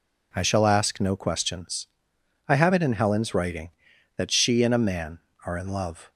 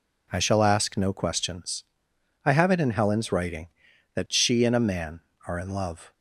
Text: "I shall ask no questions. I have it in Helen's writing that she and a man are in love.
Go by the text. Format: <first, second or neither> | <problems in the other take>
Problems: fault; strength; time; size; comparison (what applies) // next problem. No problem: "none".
neither | none